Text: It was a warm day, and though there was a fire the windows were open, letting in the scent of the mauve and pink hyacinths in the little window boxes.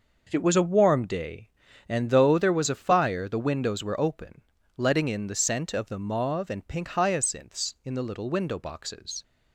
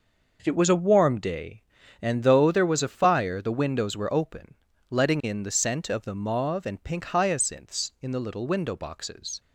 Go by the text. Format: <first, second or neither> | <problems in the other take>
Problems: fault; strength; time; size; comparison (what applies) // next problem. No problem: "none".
neither | none